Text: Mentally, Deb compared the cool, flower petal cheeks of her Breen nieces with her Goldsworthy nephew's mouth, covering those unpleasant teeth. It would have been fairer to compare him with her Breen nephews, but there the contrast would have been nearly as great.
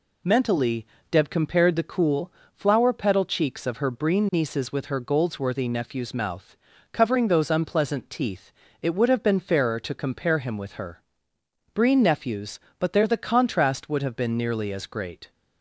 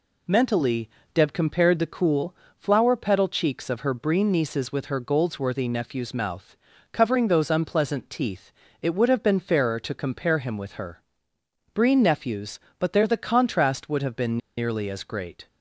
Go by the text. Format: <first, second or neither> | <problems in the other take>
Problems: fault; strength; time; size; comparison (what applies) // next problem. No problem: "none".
first | pauses between "her" and "Breen"; noticeable; at 11.0 s; 0.72 s long; noticeable in the first // pauses between "been" and "nearly"; slight; at 14.3 s; 0.19 s long